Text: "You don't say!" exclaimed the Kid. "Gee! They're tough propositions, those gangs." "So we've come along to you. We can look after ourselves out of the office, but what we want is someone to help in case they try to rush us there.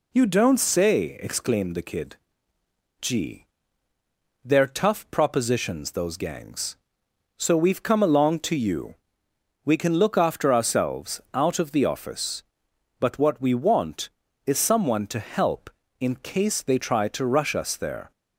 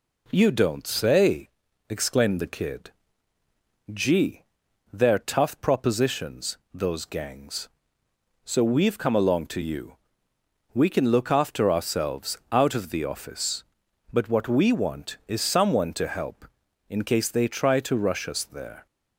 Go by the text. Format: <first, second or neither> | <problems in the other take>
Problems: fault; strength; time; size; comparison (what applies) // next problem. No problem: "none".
neither | none